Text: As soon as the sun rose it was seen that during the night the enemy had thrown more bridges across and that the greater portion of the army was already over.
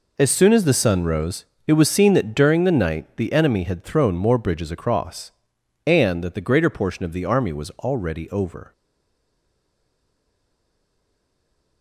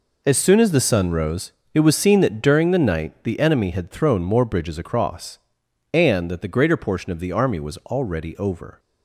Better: second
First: pauses between "rose" and "it"; slight; at 1.4 s; 0.22 s long // stays silent after the last word; strong; from 8.7 s on; 3.1 s long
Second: pauses between "rose" and "it"; slight; at 1.5 s; 0.22 s long

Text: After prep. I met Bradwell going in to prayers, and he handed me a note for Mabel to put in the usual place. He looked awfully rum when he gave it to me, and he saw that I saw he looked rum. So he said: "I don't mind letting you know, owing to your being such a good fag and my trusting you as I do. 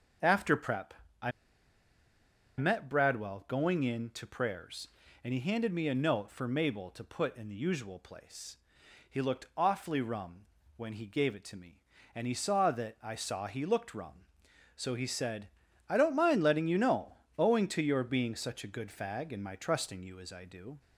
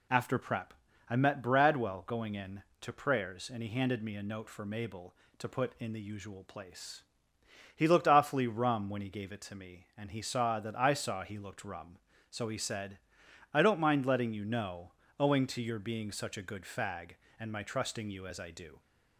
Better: second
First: starts louder than the rest; until 2.7 s; 6.5 dB // pauses between "I" and "met"; strong; at 1.3 s; 1.2 s long // pauses between "rum" and "when"; slight; at 10.4 s; 0.32 s long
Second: none

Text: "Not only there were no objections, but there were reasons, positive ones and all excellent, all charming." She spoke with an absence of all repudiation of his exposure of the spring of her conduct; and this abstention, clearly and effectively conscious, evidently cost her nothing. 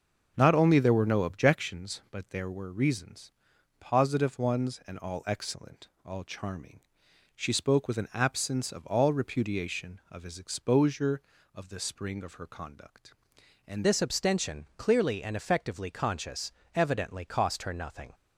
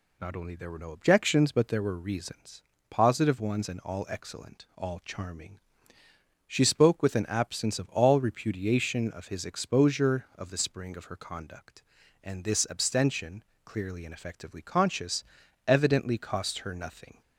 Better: second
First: starts louder than the rest; noticeable; until 1.3 s; 6 dB // changes voice at "this"; from 13.8 s on; 4.3 s long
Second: none

